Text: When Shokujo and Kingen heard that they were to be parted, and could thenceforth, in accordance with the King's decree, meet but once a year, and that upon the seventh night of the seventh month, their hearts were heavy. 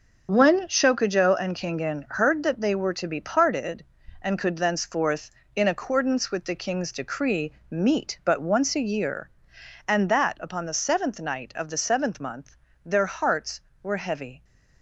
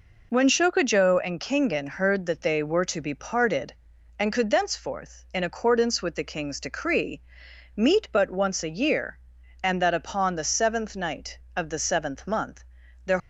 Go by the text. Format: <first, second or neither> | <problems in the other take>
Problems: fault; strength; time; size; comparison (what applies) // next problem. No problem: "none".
first | stops before "hearts were heavy"; at 13.1 s